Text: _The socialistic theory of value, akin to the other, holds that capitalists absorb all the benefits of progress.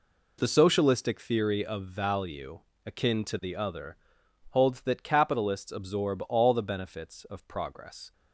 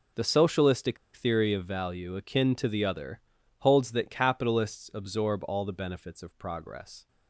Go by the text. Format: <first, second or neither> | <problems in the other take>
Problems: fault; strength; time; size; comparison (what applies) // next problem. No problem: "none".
first | pauses between "socialistic" and "theory"; slight; at 0.9 s; 0.18 s long